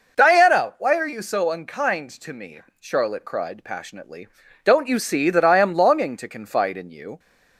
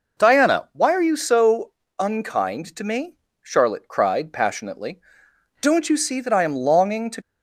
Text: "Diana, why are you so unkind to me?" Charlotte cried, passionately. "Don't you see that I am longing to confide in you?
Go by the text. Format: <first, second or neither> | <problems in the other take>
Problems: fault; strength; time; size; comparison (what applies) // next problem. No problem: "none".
first | pauses between "so" and "unkind"; slight; at 1.6 s; 0.30 s long // stops before "confide in you"; at 7.2 s